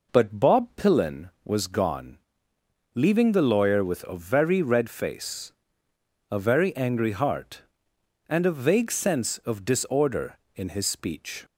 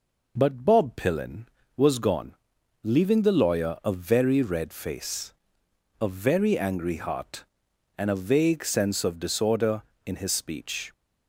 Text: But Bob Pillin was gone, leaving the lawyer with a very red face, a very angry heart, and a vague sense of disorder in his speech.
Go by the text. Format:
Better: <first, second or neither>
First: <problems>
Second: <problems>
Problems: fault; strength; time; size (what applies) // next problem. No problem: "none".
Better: first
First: none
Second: skips "with"; at 3.7 s